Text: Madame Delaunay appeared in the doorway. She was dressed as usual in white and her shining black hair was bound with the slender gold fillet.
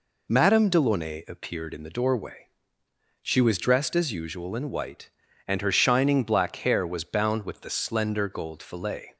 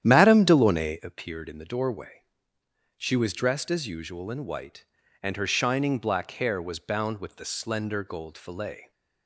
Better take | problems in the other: first | starts louder than the rest; strong; until 1.1 s; 10.5 dB

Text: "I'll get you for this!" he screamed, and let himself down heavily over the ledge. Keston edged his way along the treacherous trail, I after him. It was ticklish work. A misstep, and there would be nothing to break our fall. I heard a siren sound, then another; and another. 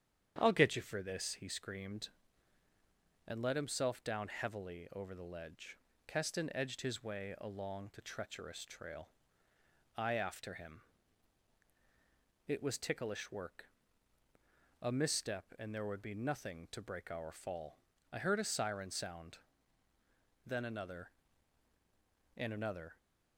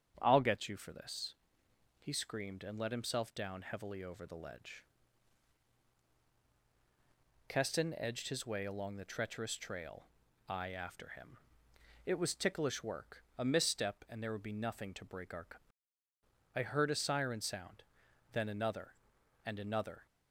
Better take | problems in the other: first | starts louder than the rest; strong; until 1.2 s; 8 dB; strong in the first // skips "fall"; at 16.0 s

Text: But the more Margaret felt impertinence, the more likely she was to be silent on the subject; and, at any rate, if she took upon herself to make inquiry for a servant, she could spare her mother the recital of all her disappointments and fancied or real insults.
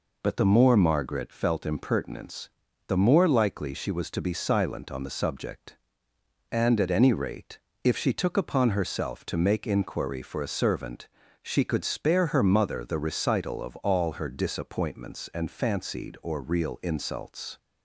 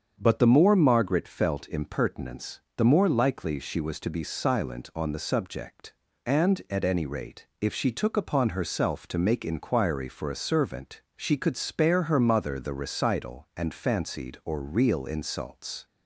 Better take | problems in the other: first | starts louder than the rest; until 1.2 s; 7 dB // skips "of all her disappointments"; at 13.5 s

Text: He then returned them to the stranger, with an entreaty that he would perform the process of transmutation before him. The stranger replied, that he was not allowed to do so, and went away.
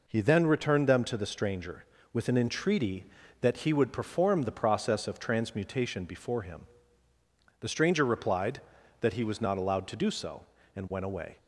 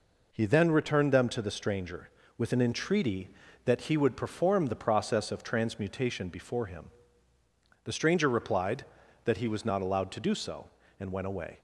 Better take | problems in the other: neither | none

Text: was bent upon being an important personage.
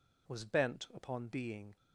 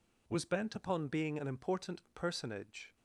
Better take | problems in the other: second | stops before "an important personage"; at 1.7 s

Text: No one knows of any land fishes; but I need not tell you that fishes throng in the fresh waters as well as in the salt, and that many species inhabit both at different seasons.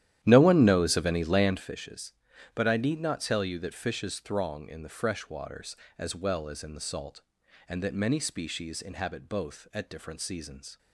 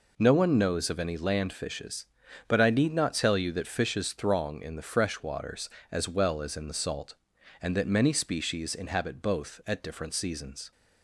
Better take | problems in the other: second | starts louder than the rest; strong; until 1.8 s; 12 dB

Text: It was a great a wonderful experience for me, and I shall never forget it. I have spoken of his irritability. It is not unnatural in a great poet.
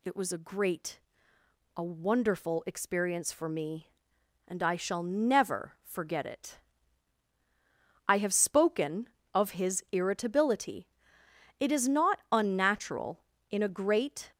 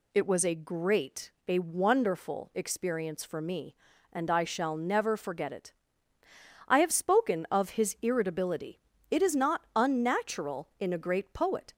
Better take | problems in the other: second | pauses between "great" and "a"; noticeable; at 0.9 s; 0.78 s long; slight in the second // stops before "poet"; at 14.3 s

